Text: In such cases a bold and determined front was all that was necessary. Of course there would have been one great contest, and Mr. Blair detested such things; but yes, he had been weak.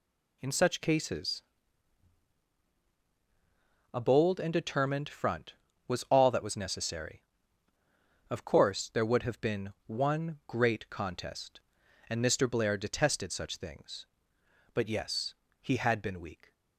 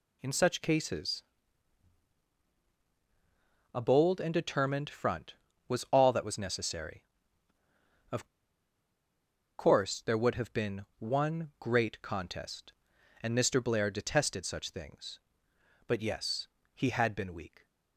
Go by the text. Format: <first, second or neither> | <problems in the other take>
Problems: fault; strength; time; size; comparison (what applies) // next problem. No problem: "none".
first | pauses between "cases" and "a"; strong; at 1.2 s; 2.5 s long; strong in the first // pauses between "Of" and "course"; strong; at 8.2 s; 1.3 s long